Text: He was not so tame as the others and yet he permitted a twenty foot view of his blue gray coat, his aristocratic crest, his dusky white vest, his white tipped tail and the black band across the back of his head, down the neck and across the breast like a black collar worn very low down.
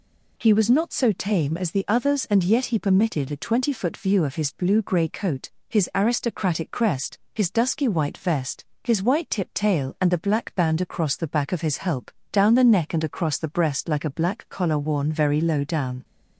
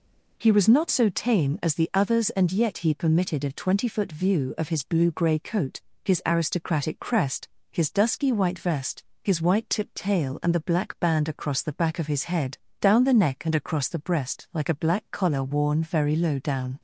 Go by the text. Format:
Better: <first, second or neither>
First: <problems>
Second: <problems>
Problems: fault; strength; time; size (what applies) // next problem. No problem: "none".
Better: second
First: says "help" for "head"; at 11.7 s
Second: none